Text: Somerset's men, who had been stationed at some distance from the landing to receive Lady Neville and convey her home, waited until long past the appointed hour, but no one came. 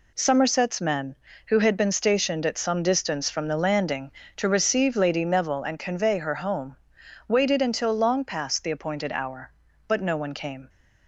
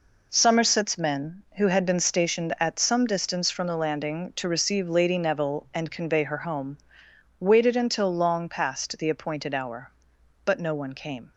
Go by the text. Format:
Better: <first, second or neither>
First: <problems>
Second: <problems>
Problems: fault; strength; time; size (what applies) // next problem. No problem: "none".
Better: neither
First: none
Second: none